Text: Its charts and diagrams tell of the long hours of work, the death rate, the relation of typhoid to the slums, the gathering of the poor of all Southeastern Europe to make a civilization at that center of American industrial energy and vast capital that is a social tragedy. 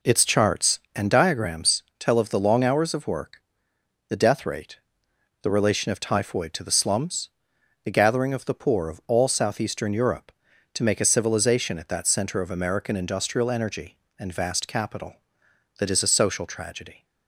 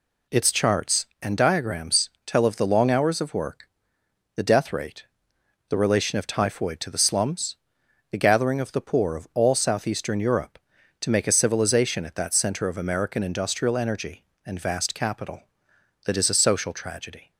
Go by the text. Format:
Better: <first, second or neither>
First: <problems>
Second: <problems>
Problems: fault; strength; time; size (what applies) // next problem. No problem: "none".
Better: second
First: starts louder than the rest; noticeable; until 1.7 s; 4.5 dB // pauses between "diagrams" and "tell"; slight; at 1.8 s; 0.16 s long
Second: pauses between "diagrams" and "tell"; slight; at 2.0 s; 0.16 s long